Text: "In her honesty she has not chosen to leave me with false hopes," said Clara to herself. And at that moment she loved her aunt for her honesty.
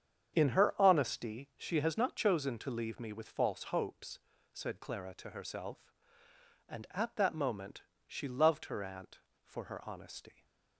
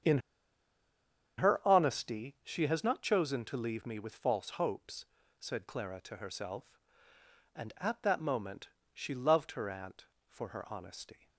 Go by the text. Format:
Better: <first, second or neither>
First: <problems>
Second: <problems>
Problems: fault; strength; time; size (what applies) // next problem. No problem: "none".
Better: first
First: starts louder than the rest; strong; until 1.4 s; 8 dB // pauses between "moment" and "she"; slight; at 7.8 s; 0.22 s long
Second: starts louder than the rest; strong; until 2.3 s; 8 dB // pauses between "In" and "her"; at 0.1 s; 1.1 s long // pauses between "moment" and "she"; slight; at 8.6 s; 0.22 s long